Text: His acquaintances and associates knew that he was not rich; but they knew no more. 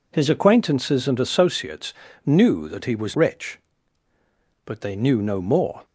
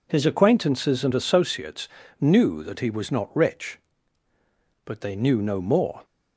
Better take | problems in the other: second | pauses between "associates" and "knew"; slight; at 1.9 s; 0.32 s long; slight in the second // skips "not"; at 3.1 s

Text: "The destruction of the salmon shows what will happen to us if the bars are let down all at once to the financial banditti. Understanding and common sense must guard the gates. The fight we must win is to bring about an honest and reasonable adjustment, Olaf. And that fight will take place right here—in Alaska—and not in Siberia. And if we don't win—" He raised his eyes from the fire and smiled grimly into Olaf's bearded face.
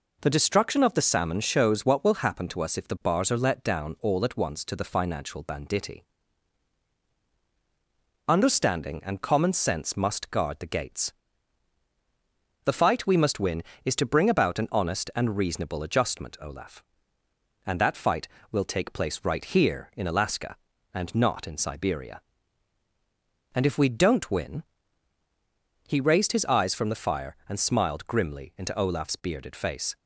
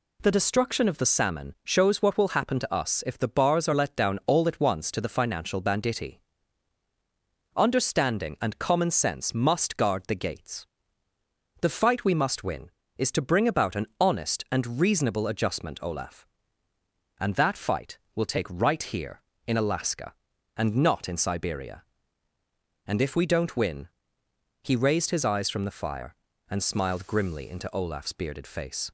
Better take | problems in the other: first | skips "place"; at 18.4 s

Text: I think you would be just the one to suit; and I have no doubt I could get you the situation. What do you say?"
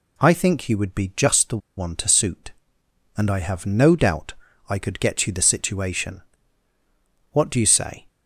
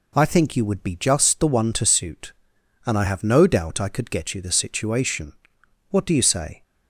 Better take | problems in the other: second | pauses between "the" and "one"; slight; at 1.5 s; 0.19 s long // pauses between "doubt" and "I"; slight; at 4.3 s; 0.34 s long

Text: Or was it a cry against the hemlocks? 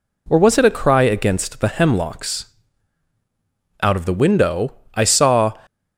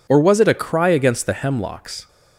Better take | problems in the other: second | goes on to say "Out of the window I saw"; strong; from 3.8 s on; 1.7 s long

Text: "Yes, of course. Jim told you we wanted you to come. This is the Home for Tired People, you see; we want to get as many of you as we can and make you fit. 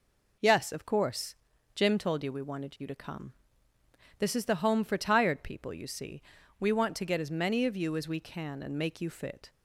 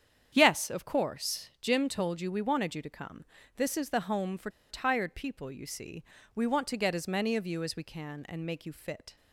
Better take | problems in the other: first | starts louder than the rest; strong; until 1.3 s; 8.5 dB // pauses between "for" and "Tired"; slight; at 4.4 s; 0.20 s long

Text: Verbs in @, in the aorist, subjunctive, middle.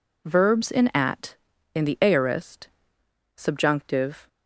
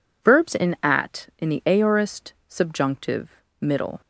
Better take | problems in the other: second | stops before "middle"; at 4.2 s

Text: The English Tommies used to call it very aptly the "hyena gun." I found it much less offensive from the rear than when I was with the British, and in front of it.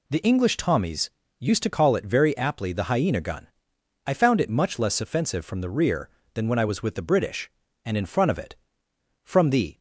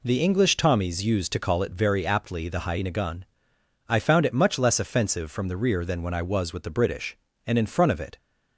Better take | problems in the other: second | pauses between "Tommies" and "used"; slight; at 1.0 s; 0.30 s long // goes on to say "From the"; from 9.2 s on; 0.54 s long

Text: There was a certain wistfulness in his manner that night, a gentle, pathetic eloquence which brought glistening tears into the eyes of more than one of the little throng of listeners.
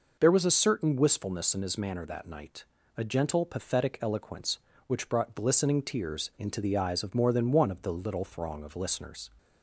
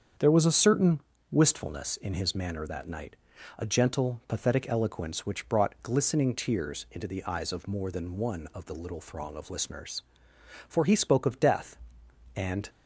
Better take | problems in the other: first | starts louder than the rest; strong; until 1.4 s; 7.5 dB // pauses between "certain" and "wistfulness"; slight; at 1.0 s; 0.30 s long // goes on to say "For he spoke of death and"; strong; from 10.6 s on; 2.0 s long

